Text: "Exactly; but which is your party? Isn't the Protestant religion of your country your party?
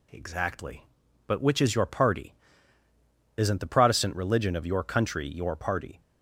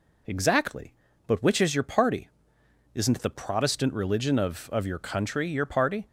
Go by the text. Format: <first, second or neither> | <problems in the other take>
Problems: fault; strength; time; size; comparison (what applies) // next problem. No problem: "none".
first | says "of" twice; at 4.7 s